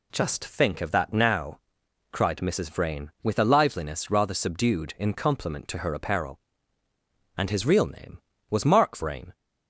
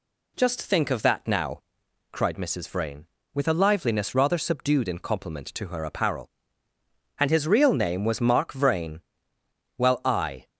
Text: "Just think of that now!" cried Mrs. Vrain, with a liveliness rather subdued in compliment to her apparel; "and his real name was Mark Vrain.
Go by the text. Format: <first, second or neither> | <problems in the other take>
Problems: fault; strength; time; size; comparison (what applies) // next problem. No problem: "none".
first | goes on to say "Well I"; noticeable; from 9.7 s on; 0.70 s long